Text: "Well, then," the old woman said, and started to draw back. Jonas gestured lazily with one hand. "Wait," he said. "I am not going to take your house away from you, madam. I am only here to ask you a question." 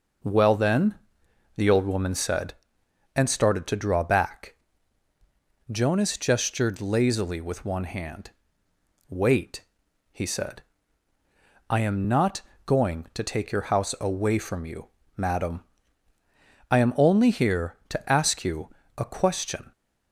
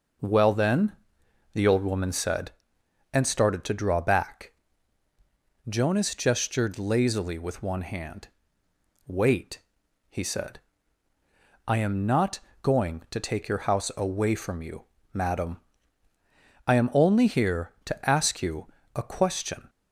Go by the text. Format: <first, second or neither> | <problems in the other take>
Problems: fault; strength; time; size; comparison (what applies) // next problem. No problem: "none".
neither | pauses between "not" and "going"; slight; the same in both // pauses between "you" and "a"; slight; the same in both